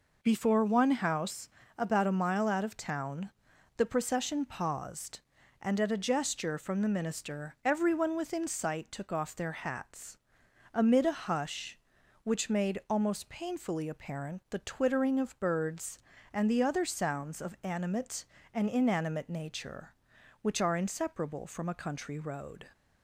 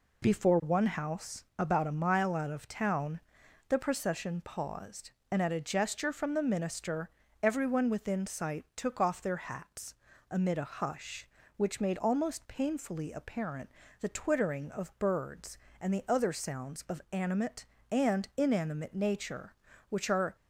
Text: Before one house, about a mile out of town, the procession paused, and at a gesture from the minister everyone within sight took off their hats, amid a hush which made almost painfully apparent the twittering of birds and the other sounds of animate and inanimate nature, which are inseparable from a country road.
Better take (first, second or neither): first